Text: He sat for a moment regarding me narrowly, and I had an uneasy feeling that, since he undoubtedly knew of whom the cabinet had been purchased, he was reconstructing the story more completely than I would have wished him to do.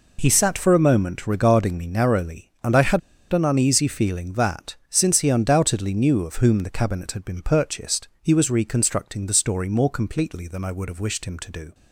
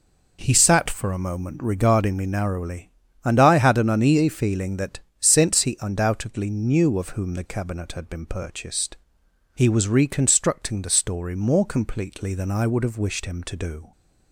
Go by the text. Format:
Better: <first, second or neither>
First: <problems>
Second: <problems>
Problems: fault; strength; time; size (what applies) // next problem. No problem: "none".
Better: second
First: pauses between "had" and "an"; slight; at 3.0 s; 0.32 s long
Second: none